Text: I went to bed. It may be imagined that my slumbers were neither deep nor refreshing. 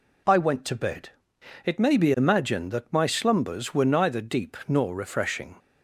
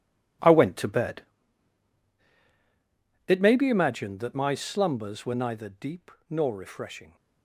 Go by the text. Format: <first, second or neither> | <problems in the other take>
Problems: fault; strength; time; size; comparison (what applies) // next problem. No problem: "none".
first | gets quieter; strong; throughout; 13 dB // pauses between "deep" and "nor"; slight; at 6.1 s; 0.20 s long